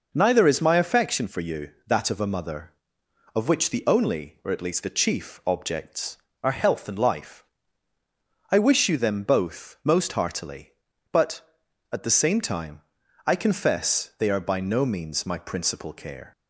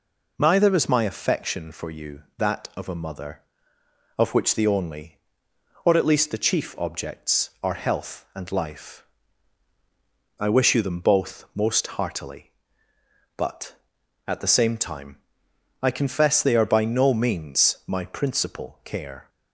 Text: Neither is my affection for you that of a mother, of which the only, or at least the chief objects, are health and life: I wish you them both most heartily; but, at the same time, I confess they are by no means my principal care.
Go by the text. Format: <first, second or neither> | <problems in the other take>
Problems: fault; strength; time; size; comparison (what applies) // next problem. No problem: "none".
neither | none